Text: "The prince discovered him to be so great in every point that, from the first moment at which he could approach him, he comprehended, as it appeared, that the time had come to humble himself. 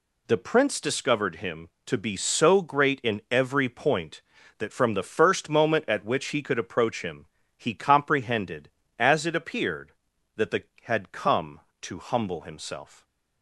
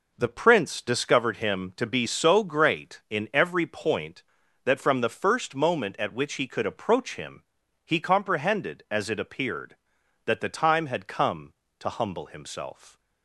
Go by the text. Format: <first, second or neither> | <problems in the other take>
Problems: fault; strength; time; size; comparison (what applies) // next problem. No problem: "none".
second | skips "time"; at 10.7 s